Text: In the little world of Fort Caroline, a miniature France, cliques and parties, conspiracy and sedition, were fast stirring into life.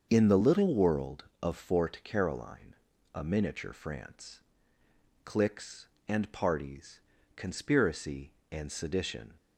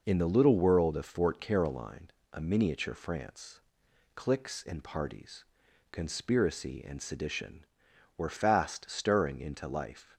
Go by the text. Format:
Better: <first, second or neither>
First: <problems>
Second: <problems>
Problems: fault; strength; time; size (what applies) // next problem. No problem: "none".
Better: second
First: starts louder than the rest; until 1.1 s; 6.5 dB // stops before "were fast stirring into life"; at 9.3 s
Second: none